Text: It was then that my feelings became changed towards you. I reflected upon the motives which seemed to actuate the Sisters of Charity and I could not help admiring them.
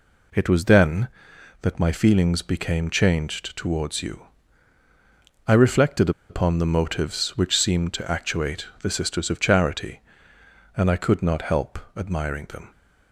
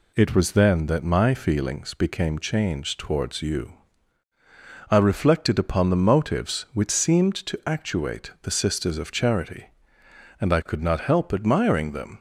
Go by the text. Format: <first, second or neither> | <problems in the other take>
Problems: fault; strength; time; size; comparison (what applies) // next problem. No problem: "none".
second | pauses between "reflected" and "upon"; slight; at 6.1 s; 0.19 s long // pauses between "actuate" and "the"; slight; at 8.6 s; 0.16 s long // pauses between "help" and "admiring"; slight; at 11.7 s; 0.18 s long